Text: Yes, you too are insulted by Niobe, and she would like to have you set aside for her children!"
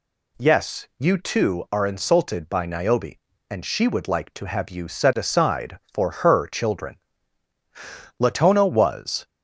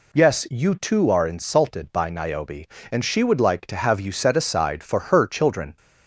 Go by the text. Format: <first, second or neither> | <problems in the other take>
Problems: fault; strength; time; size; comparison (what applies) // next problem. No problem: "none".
second | goes on to say "Latona was"; noticeable; from 8.1 s on; 1.0 s long